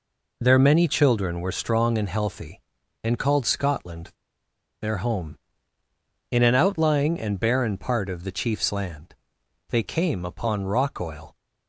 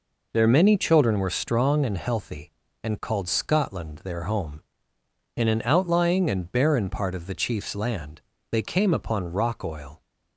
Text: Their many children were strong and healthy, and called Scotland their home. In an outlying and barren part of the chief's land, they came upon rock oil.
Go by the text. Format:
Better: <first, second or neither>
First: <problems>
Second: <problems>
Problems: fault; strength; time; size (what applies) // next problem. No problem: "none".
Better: second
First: pauses between "Scotland" and "their"; noticeable; at 4.1 s; 0.69 s long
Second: none